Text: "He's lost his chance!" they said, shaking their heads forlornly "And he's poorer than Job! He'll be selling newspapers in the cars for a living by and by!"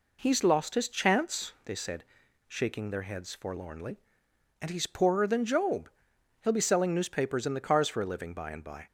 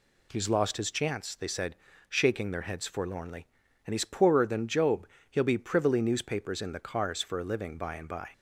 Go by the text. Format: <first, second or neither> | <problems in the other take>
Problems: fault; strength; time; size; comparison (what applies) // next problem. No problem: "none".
first | says "privily" for "selling"; at 5.5 s